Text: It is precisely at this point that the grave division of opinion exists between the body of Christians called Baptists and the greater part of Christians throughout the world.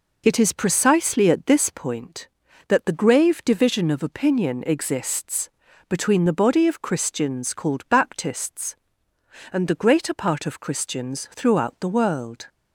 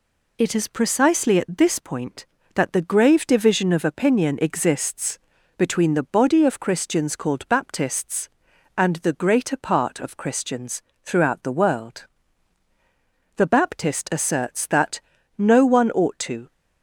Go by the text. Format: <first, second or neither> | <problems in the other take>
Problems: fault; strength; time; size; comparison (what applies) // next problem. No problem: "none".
first | pauses between "exists" and "between"; at 5.1 s; 0.38 s long; slight in the first // pauses between "Christians" and "throughout"; slight; at 10.8 s; 0.22 s long // goes on to say "The Baptist asserts that no one ought to"; strong; from 13.3 s on; 3.1 s long